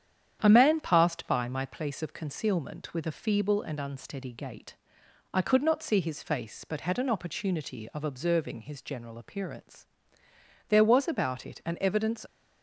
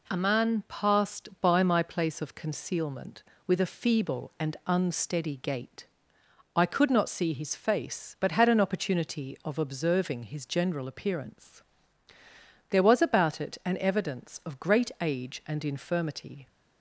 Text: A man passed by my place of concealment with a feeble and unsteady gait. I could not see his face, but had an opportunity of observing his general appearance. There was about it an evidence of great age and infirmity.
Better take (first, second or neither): second